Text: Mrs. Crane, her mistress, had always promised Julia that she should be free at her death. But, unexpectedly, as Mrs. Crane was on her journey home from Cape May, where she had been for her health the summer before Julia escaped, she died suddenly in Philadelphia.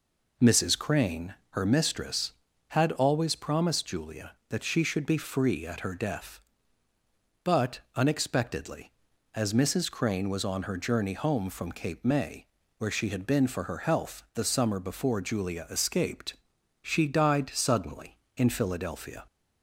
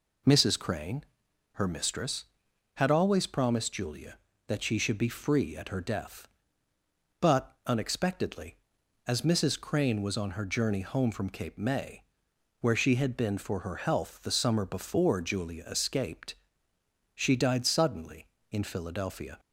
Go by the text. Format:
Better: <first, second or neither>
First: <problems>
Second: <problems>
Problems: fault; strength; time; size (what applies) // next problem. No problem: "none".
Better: neither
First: none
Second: none